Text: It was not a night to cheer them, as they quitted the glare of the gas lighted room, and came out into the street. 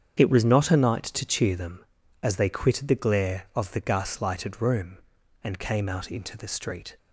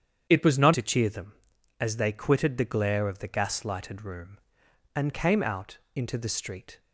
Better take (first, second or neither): first